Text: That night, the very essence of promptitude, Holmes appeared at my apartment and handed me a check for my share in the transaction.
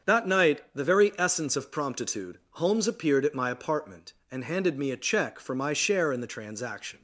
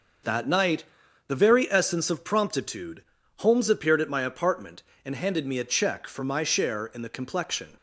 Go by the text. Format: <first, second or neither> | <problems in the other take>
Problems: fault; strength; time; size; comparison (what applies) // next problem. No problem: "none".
first | starts louder than the rest; noticeable; until 1.6 s; 6 dB; strong in the first // says "complexion" for "transaction"; at 7.1 s